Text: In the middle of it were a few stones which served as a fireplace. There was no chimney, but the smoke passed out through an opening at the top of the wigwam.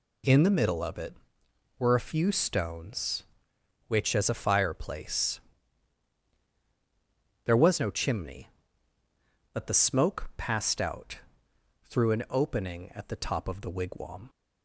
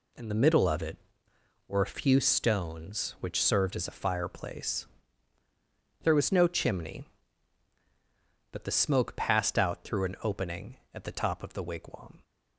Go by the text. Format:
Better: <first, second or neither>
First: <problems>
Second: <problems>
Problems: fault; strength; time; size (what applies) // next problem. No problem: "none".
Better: second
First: skips "served"; at 4.1 s // pauses between "out" and "through"; noticeable; at 11.1 s; 0.66 s long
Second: none